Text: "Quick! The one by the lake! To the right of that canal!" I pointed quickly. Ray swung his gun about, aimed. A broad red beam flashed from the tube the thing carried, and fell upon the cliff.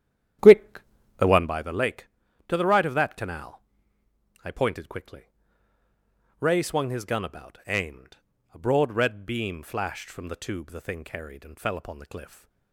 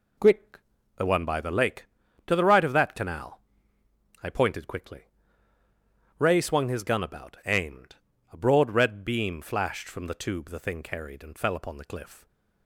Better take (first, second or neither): second